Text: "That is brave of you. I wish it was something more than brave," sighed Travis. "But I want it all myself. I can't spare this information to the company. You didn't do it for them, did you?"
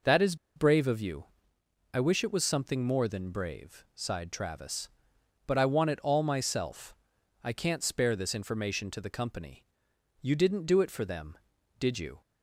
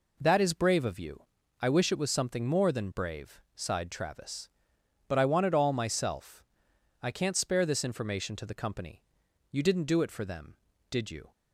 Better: second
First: pauses between "is" and "brave"; slight; at 0.3 s; 0.21 s long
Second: none

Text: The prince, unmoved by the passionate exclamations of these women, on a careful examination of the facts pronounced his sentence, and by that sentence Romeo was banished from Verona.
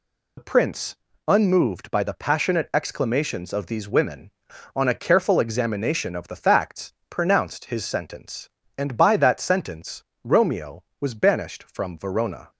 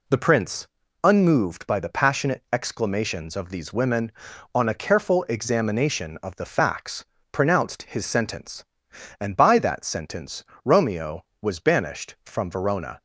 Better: second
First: loses the start of "The"; at 0.3 s; 55 ms // pauses between "facts" and "pronounced"; slight; at 6.9 s; 0.18 s long // pauses between "sentence" and "Romeo"; slight; at 10.0 s; 0.22 s long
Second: pauses between "facts" and "pronounced"; slight; at 7.0 s; 0.28 s long // pauses between "sentence" and "Romeo"; slight; at 10.4 s; 0.20 s long

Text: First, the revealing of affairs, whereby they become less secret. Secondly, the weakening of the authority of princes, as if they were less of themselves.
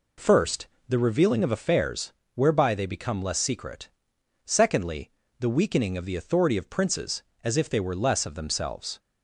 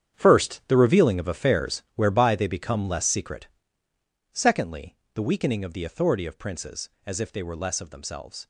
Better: first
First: none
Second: gets quieter; strong; throughout; 12.5 dB

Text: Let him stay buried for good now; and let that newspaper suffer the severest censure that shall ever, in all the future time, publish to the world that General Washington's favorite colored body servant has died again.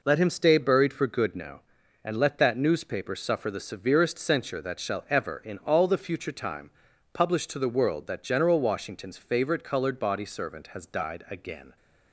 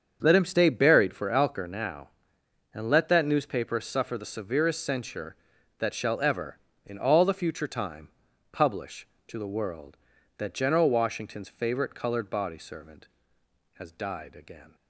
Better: first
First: none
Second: starts louder than the rest; strong; until 1.2 s; 7 dB // says "alker" for "good"; at 1.3 s

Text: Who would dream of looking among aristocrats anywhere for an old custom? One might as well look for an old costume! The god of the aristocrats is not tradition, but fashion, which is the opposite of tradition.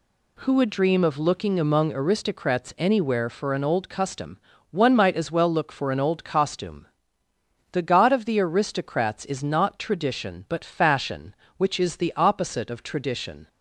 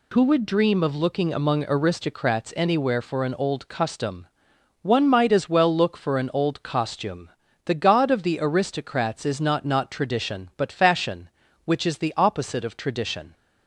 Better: first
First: none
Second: says "not" twice; at 9.6 s

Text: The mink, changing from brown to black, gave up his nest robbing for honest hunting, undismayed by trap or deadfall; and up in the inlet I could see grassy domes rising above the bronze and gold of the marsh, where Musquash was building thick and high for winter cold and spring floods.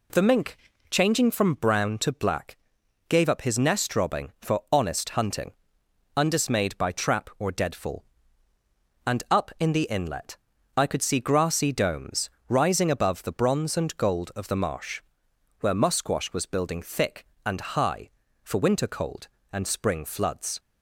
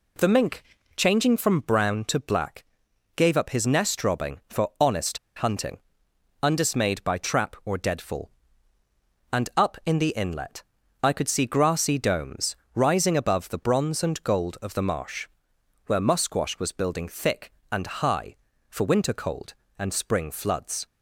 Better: first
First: pauses between "inlet" and "I"; at 10.3 s; 0.38 s long // pauses between "domes" and "rising"; slight; at 12.3 s; 0.18 s long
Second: pauses between "honest" and "hunting"; slight; at 5.1 s; 0.18 s long // pauses between "inlet" and "I"; at 10.6 s; 0.38 s long // pauses between "domes" and "rising"; slight; at 12.5 s; 0.18 s long

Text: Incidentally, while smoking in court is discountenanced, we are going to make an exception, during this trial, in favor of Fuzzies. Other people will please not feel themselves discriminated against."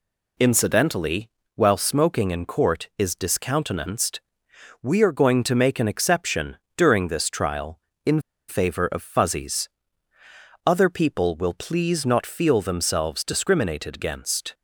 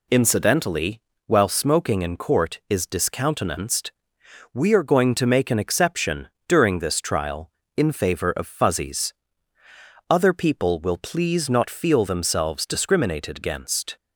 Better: second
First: pauses between "in" and "favor"; slight; at 8.2 s; 0.27 s long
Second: none

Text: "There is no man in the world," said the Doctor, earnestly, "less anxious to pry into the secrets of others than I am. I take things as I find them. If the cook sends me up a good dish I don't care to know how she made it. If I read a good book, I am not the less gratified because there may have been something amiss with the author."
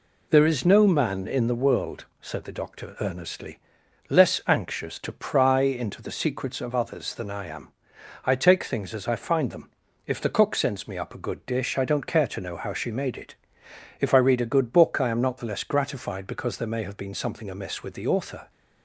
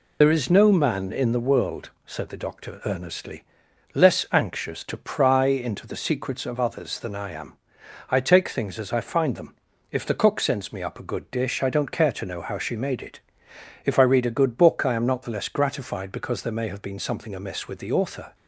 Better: first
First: none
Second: loses the start of "There"; at 0.2 s; 60 ms

